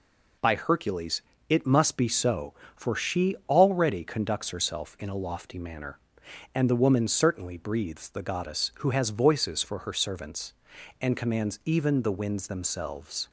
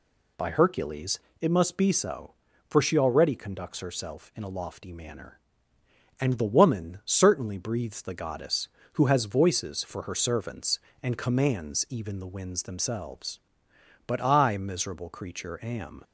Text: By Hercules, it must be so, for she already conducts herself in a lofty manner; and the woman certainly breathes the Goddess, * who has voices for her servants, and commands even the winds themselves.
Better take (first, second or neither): first